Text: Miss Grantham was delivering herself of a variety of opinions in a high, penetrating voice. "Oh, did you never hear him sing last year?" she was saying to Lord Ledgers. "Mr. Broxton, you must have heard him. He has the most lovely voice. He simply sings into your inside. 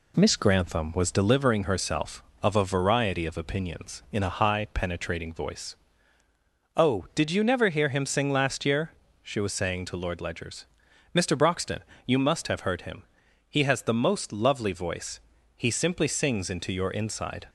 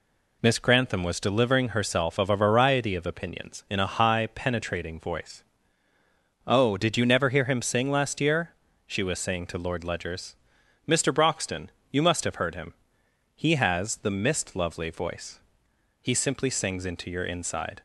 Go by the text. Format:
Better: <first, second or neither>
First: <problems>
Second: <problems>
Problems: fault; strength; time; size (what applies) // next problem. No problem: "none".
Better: first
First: none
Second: says "mist" for "most"; at 14.1 s